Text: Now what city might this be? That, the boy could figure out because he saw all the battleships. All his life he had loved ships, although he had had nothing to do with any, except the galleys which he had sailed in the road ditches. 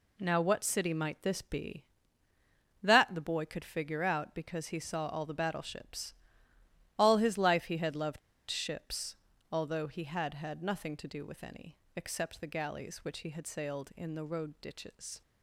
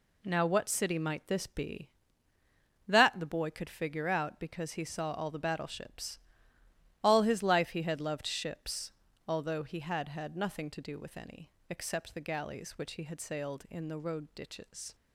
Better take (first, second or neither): second